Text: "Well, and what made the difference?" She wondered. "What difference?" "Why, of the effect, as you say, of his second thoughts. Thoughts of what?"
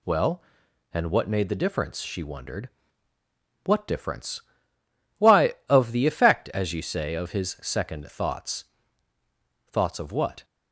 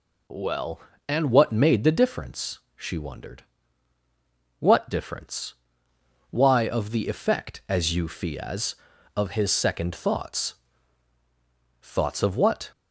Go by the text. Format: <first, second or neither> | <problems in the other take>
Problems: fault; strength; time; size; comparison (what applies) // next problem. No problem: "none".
first | says "fias" for "say"; at 8.0 s